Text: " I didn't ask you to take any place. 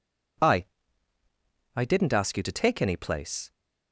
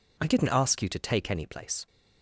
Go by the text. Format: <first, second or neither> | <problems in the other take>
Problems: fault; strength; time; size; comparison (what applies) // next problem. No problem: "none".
second | says "I" twice; at 1.7 s